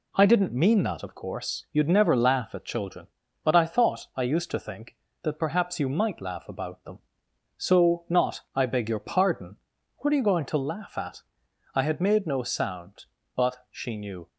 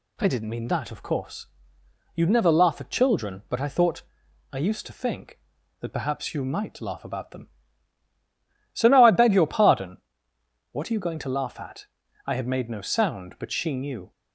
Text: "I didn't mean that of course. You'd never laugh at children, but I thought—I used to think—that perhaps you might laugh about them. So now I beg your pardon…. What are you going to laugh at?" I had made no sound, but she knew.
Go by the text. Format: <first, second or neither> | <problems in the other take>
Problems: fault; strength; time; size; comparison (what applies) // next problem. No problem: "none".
second | says "not" for "now"; at 8.0 s